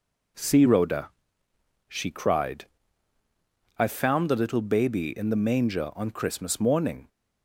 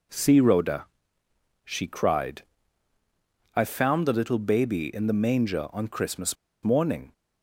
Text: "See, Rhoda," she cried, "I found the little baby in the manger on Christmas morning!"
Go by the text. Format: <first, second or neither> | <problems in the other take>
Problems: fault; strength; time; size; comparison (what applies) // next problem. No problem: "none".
first | pauses between "Christmas" and "morning"; slight; at 6.3 s; 0.27 s long